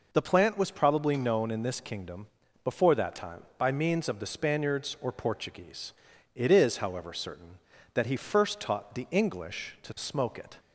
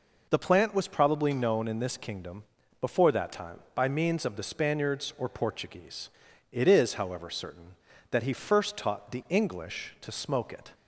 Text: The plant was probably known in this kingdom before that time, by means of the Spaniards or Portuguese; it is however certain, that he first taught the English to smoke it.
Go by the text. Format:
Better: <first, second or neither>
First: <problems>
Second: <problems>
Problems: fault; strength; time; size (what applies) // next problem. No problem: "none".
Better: neither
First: pauses between "kingdom" and "before"; slight; at 2.2 s; 0.36 s long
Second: pauses between "kingdom" and "before"; slight; at 2.4 s; 0.36 s long